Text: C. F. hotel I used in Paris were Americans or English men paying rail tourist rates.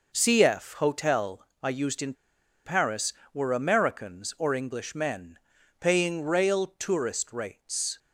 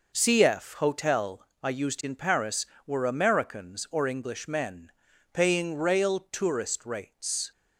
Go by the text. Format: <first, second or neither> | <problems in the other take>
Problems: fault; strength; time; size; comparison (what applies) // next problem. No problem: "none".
second | pauses between "hotel" and "I"; slight; at 1.4 s; 0.16 s long; slight in the second // pauses between "in" and "Paris"; noticeable; at 2.1 s; 0.51 s long // pauses between "men" and "paying"; at 5.3 s; 0.44 s long; also in the second